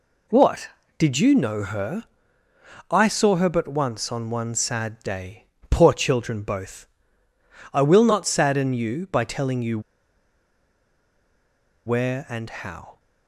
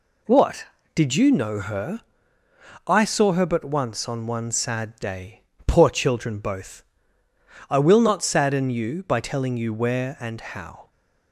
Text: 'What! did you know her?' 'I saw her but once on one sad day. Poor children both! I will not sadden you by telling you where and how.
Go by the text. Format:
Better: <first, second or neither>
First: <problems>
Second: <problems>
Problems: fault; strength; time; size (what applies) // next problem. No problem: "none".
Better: second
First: pauses between "you" and "where"; strong; at 9.7 s; 2.0 s long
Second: none